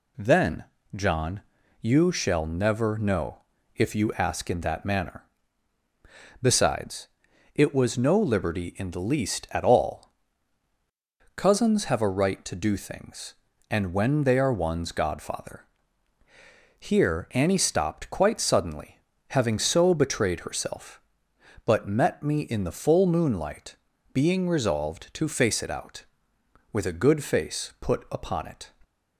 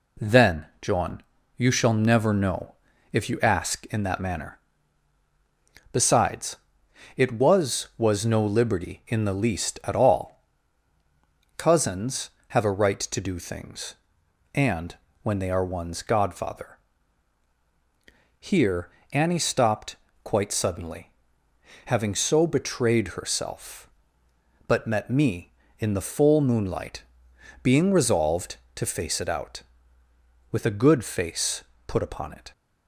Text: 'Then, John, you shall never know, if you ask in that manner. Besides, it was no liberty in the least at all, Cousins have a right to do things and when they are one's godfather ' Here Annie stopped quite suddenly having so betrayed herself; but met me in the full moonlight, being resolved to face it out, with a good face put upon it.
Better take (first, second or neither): first